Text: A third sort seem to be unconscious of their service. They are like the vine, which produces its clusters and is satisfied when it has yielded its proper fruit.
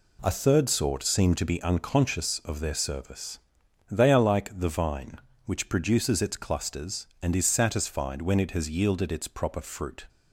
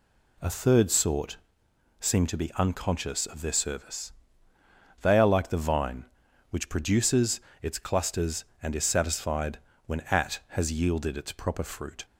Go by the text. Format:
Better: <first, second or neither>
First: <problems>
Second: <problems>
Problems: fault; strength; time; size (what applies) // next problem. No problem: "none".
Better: first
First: none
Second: pauses between "sort" and "seem"; noticeable; at 1.3 s; 0.62 s long // pauses between "produces" and "its"; slight; at 7.4 s; 0.20 s long // pauses between "satisfied" and "when"; slight; at 9.5 s; 0.28 s long // says "at" for "it"; at 10.1 s